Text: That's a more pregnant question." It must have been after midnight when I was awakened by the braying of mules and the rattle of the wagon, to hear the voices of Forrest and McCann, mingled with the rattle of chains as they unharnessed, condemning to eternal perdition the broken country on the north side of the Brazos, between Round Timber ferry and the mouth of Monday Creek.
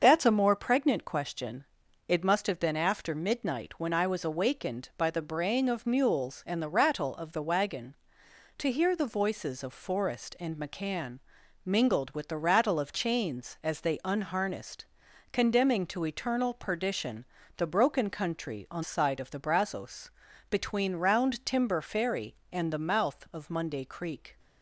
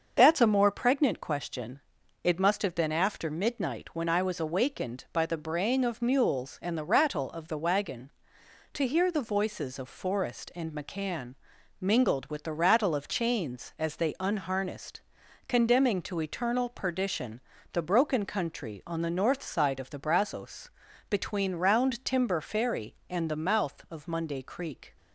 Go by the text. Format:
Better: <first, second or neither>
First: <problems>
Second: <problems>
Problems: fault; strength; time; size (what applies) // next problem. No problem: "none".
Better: second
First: starts louder than the rest; until 1.0 s; 6.5 dB // pauses between "perdition" and "the"; slight; at 17.2 s; 0.30 s long // skips "the north"; at 18.8 s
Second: starts louder than the rest; until 1.1 s; 6.5 dB // pauses between "perdition" and "the"; slight; at 17.4 s; 0.30 s long